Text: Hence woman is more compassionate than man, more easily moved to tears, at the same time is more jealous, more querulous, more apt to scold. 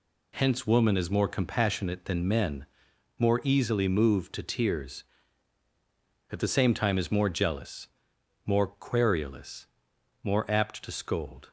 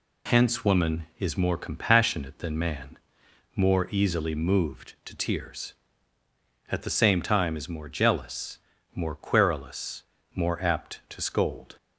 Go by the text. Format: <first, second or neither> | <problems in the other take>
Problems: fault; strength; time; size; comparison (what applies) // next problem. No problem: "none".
second | says "men" for "man"; at 2.2 s